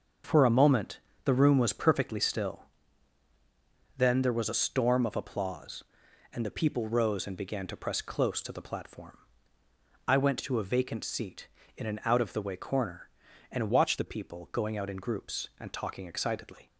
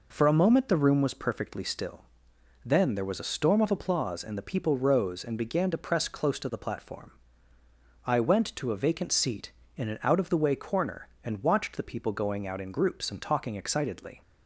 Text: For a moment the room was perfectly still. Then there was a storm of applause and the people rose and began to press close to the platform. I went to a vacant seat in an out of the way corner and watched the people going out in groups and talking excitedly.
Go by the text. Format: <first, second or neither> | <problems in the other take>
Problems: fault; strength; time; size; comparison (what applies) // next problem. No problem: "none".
second | starts louder than the rest; until 1.5 s; 6.5 dB // pauses between "moment" and "the"; slight; at 0.9 s; 0.28 s long // changes voice from "watched" to "the"; from 13.6 to 14.0 s; 0.4 s long